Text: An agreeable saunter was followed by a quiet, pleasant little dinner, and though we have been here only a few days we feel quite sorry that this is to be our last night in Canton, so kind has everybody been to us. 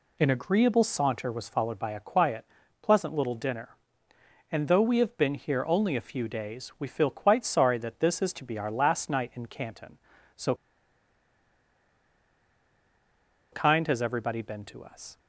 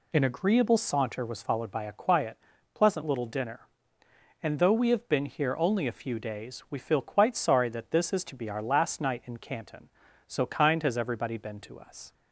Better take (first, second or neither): second